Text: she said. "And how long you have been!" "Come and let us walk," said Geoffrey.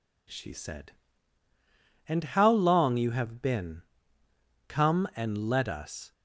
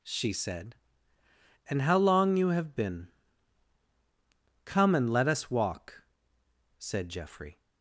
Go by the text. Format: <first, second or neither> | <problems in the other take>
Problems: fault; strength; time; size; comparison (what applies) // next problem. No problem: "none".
second | stops before "walk said Geoffrey"; at 6.1 s